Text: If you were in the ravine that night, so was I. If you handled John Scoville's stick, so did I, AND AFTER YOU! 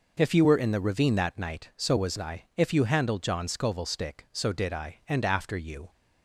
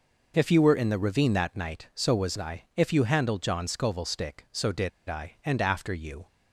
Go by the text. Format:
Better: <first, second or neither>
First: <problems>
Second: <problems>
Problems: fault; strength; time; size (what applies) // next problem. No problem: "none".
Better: first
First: none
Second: pauses between "did" and "I"; slight; at 4.8 s; 0.18 s long